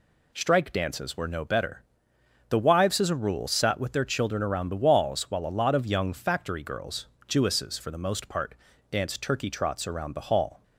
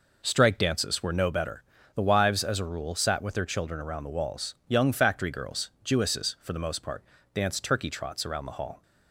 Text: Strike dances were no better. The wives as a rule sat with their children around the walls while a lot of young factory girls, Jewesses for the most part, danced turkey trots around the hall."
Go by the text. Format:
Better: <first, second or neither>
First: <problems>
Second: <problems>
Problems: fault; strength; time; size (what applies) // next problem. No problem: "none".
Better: first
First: none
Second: skips "while a lot of"; at 4.6 s